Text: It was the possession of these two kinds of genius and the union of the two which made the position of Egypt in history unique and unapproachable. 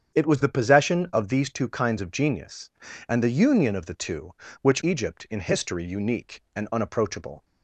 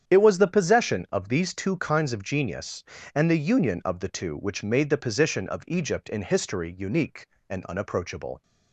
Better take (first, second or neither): second